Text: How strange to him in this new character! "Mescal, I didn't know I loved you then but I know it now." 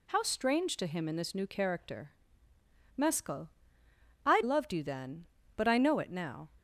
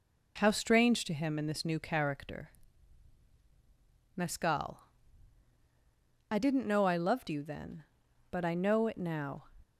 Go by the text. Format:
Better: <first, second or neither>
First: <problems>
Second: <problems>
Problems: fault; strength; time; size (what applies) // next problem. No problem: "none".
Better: second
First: skips "didn't know I"; at 4.4 s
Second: none